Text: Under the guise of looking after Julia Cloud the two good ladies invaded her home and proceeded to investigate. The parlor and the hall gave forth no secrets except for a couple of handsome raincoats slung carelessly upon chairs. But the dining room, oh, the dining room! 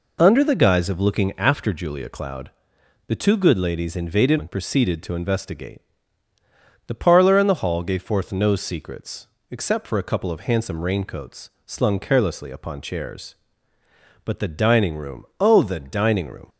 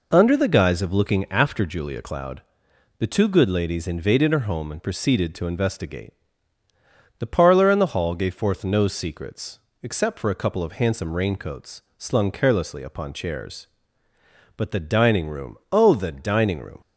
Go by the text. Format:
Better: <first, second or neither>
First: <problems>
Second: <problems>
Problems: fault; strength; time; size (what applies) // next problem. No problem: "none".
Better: second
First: pauses between "Cloud" and "the"; noticeable; at 2.5 s; 0.56 s long // skips "her home"; at 4.3 s // pauses between "secrets" and "except"; slight; at 9.2 s; 0.22 s long // pauses between "raincoats" and "slung"; slight; at 11.4 s; 0.16 s long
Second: pauses between "Cloud" and "the"; noticeable; at 2.4 s; 0.56 s long // pauses between "secrets" and "except"; slight; at 9.5 s; 0.22 s long // pauses between "raincoats" and "slung"; slight; at 11.8 s; 0.16 s long